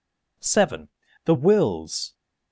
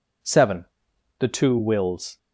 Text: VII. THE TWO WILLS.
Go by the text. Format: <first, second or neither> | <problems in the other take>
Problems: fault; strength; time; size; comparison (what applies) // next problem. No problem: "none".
second | skips "TWO"; at 1.3 s